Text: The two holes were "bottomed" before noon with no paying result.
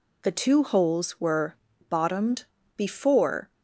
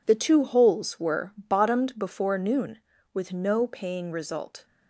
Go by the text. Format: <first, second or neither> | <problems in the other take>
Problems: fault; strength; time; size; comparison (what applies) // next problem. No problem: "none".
second | pauses between "were" and "bottomed"; slight; at 1.5 s; 0.36 s long // pauses between "bottomed" and "before"; slight; at 2.4 s; 0.30 s long // stops before "noon with no paying result"; at 3.5 s